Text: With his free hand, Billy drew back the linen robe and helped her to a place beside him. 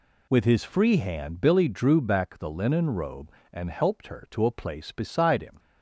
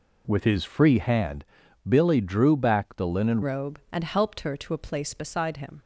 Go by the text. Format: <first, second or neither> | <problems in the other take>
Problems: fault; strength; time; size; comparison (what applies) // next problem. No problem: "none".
first | changes voice at "robe"; from 3.4 s on; 2.4 s long